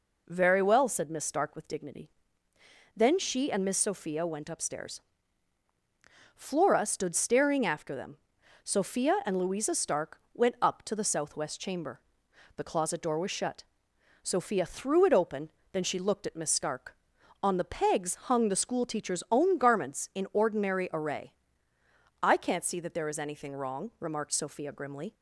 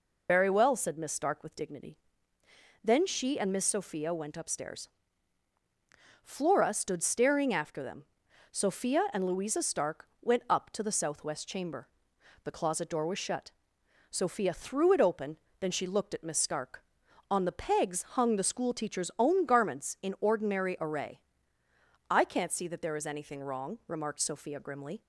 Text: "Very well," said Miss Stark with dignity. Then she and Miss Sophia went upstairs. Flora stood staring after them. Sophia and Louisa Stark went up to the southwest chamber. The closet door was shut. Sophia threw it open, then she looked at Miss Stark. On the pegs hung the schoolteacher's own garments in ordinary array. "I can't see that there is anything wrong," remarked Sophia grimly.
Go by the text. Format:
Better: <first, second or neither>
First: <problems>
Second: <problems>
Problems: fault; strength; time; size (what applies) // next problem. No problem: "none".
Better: first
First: none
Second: loses the start of "Very"; at 0.2 s; 145 ms